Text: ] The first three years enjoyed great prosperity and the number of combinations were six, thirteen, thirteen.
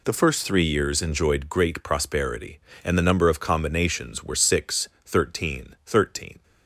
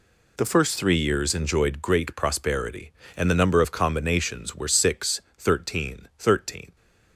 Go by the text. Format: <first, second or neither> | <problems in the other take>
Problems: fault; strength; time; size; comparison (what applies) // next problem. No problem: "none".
neither | none